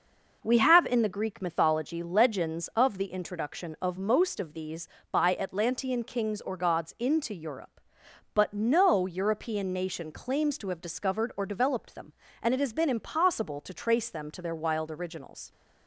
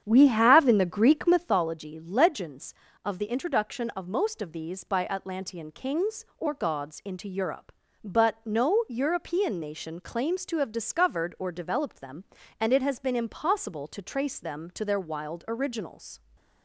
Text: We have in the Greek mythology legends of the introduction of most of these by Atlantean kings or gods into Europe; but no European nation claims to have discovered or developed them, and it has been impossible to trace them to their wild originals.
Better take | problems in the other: first | starts louder than the rest; strong; until 1.6 s; 8.5 dB

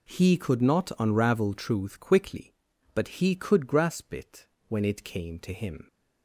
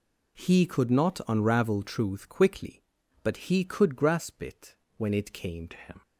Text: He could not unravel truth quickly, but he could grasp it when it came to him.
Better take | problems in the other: first | pauses between "it" and "when"; slight; at 4.7 s; 0.22 s long; slight in the first // changes voice at "to"; from 5.7 s on; 0.3 s long

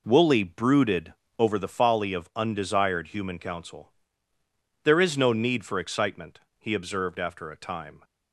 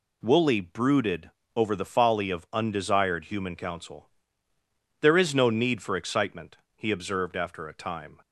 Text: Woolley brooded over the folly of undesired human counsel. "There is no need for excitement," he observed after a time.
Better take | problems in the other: second | starts louder than the rest; noticeable; until 1.6 s; 4 dB // pauses between "brooded" and "over"; slight; at 1.1 s; 0.26 s long; slight in the second

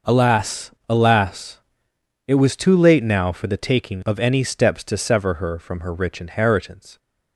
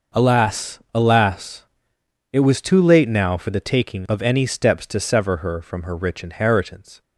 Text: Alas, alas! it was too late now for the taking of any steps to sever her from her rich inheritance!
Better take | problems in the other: neither | none

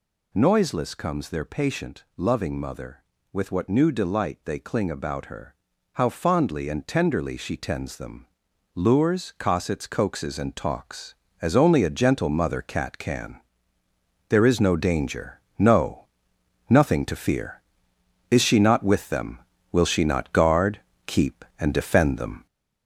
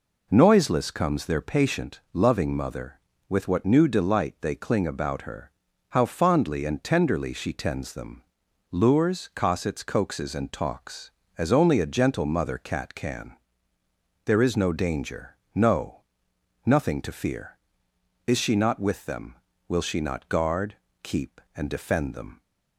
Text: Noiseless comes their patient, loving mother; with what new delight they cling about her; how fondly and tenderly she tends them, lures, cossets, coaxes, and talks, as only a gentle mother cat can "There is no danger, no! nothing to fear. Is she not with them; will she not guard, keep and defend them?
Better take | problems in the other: second | gets louder; noticeable; throughout; 4 dB // pauses between "can" and "There"; noticeable; at 13.4 s; 0.88 s long; noticeable in the second

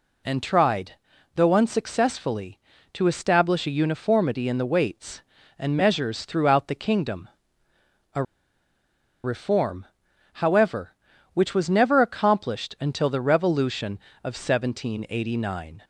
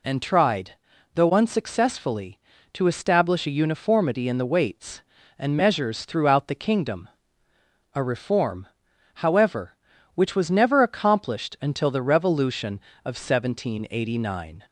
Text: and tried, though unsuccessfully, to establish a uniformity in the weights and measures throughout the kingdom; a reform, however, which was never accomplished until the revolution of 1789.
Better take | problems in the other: second | pauses between "a" and "reform"; at 8.2 s; 1.0 s long

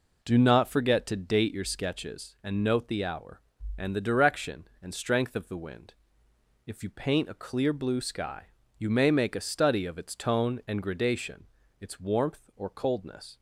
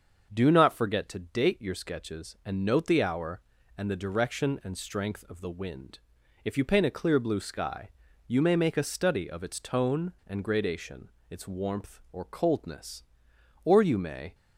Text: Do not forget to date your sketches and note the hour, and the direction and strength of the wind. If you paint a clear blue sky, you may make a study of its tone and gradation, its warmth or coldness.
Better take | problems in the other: first | starts louder than the rest; until 1.3 s; 6.5 dB // goes on to say "Or you may"; noticeable; from 13.6 s on; 0.70 s long

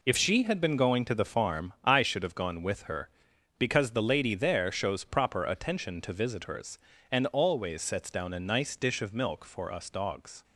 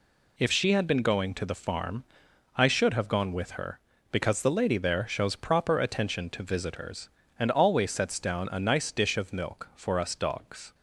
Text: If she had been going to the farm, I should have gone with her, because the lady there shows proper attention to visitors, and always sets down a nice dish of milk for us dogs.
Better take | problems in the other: neither | none

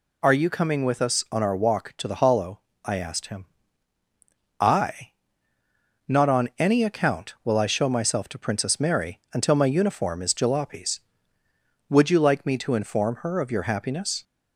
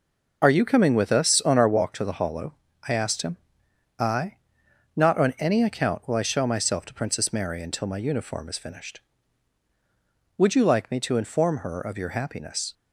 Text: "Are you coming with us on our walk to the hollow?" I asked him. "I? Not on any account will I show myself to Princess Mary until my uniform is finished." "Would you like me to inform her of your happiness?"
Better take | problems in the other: second | says "jalopies" for "finished"; at 10.3 s

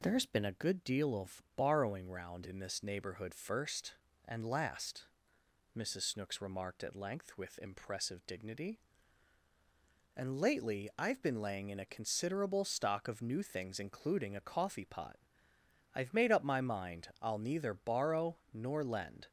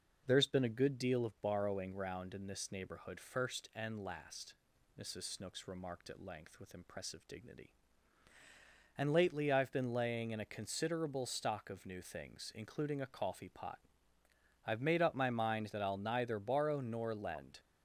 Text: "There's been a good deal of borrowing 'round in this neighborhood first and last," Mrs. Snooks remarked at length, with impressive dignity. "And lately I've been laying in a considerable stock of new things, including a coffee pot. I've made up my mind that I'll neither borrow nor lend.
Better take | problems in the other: second | skips "that"; at 17.1 s

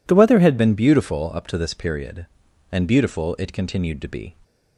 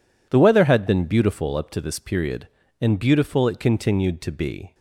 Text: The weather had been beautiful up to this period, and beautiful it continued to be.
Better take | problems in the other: second | changes voice at "been"; from 0.5 s on; 3.8 s long

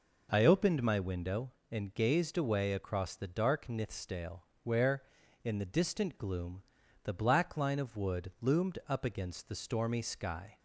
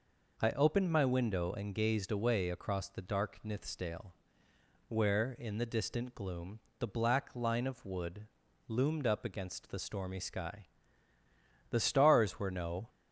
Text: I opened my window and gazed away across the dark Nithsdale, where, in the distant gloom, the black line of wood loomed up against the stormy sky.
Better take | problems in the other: first | pauses between "wood" and "loomed"; at 8.2 s; 0.42 s long // goes on to say "The stars were no"; noticeable; from 11.7 s on; 1.1 s long

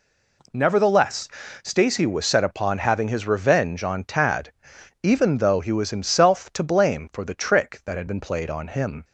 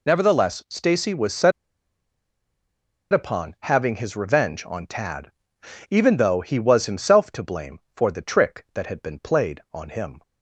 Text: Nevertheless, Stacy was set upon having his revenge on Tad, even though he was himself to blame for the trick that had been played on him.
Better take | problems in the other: first | pauses between "set" and "upon"; strong; at 1.5 s; 1.6 s long

